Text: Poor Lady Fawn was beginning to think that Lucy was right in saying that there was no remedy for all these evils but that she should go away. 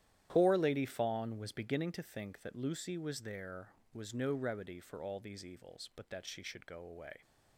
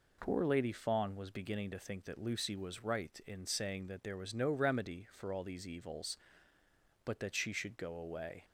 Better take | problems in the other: second | starts louder than the rest; strong; until 1.3 s; 11.5 dB // skips "right in saying that"; at 3.2 s

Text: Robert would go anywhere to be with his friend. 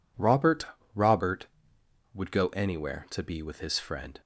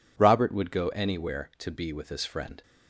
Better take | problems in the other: second | says "Robert" twice; at 0.9 s

